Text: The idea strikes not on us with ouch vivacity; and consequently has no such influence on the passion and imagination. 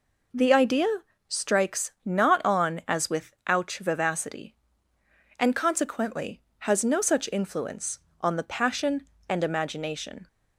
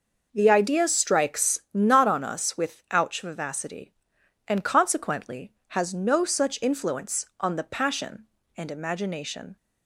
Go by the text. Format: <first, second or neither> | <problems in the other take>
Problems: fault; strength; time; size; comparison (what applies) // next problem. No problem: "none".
second | pauses between "idea" and "strikes"; at 0.8 s; 0.40 s long // says "as" for "us"; at 2.8 s // pauses between "with" and "ouch"; slight; at 3.3 s; 0.16 s long